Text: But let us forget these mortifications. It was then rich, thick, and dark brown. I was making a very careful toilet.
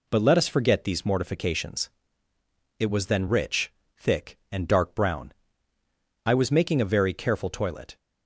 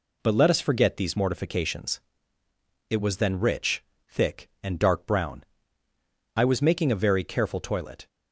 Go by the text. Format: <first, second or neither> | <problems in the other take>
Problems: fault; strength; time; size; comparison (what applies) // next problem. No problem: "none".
neither | none